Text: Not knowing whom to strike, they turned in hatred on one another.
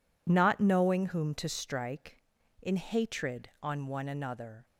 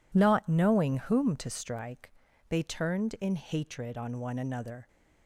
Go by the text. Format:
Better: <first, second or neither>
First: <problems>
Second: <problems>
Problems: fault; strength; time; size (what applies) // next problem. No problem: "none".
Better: second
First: skips "they turned"; at 2.4 s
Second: none